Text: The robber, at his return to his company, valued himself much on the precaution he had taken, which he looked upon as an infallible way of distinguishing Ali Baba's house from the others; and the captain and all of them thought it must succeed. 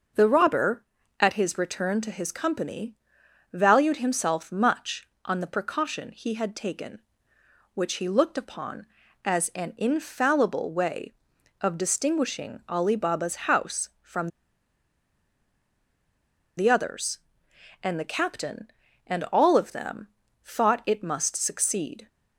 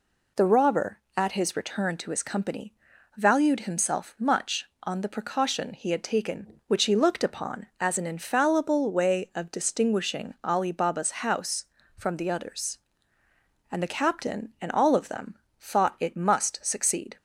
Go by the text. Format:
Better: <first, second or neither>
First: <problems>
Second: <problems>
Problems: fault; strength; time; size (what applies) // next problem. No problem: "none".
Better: second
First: starts louder than the rest; noticeable; until 1.5 s; 6 dB // pauses between "from" and "the"; strong; at 14.2 s; 2.2 s long // pauses between "them" and "thought"; slight; at 20.0 s; 0.34 s long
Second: pauses between "them" and "thought"; slight; at 15.3 s; 0.20 s long